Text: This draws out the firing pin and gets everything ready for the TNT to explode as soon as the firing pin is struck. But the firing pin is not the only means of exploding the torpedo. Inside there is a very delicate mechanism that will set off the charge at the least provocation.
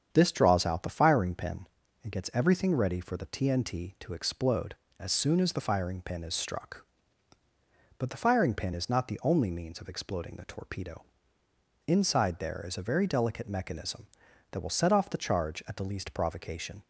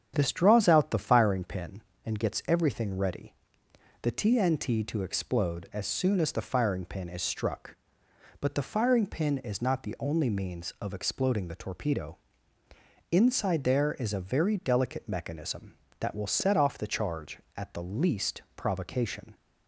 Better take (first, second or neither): first